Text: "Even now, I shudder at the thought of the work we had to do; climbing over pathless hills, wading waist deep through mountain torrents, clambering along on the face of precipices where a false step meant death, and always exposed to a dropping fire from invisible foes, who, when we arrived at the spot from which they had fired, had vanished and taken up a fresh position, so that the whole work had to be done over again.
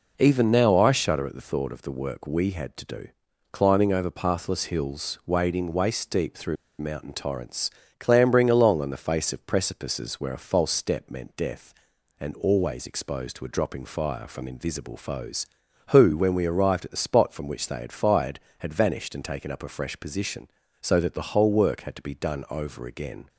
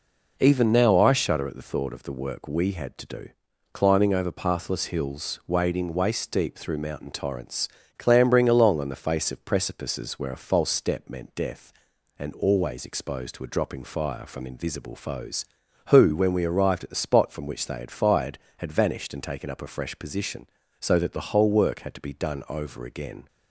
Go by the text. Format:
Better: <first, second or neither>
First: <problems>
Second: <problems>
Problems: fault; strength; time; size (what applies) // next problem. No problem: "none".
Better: second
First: pauses between "through" and "mountain"; slight; at 6.5 s; 0.23 s long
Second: none